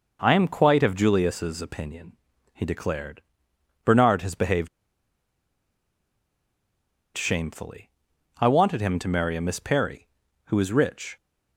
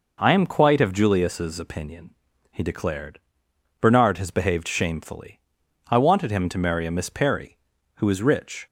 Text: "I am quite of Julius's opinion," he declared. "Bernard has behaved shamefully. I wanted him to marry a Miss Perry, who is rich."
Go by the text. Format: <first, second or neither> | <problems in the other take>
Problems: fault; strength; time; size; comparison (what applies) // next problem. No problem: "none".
second | pauses between "behaved" and "shamefully"; strong; at 4.6 s; 2.4 s long